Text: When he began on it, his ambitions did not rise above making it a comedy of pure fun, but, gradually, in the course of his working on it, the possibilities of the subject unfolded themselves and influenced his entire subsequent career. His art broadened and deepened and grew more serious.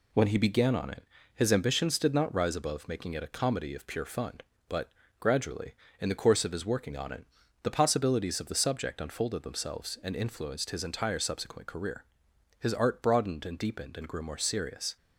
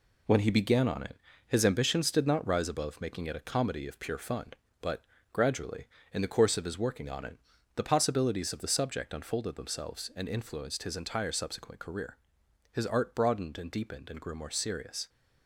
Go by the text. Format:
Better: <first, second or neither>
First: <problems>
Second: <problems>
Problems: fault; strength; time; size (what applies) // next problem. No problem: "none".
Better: first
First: none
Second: gets quieter; throughout; 6.5 dB